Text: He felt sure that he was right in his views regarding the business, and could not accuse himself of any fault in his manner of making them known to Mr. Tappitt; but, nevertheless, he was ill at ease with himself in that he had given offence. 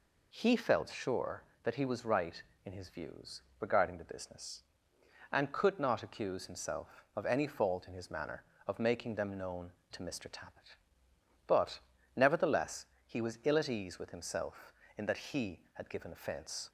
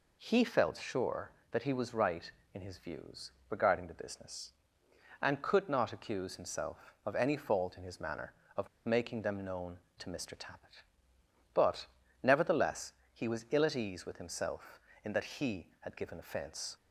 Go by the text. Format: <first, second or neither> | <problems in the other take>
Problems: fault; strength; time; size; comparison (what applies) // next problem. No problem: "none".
first | pauses between "views" and "regarding"; slight; at 3.3 s; 0.18 s long; slight in the first // pauses between "of" and "making"; slight; at 8.6 s; 0.18 s long